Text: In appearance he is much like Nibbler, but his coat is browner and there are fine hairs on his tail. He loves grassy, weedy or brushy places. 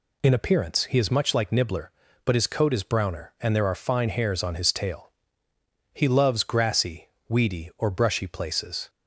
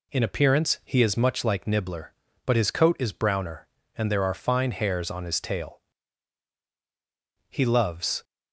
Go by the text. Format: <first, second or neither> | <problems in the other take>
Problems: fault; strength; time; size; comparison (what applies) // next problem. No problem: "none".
first | stops before "grassy weedy or brushy places"; at 8.2 s